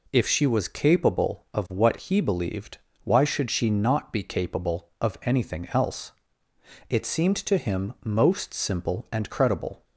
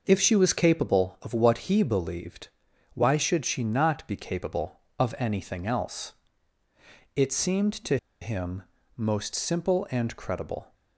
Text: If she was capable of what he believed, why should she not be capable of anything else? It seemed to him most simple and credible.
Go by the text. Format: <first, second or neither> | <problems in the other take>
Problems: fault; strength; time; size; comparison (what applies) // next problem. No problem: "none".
first | pauses between "to" and "him"; slight; at 7.9 s; 0.24 s long // pauses between "him" and "most"; slight; at 8.6 s; 0.34 s long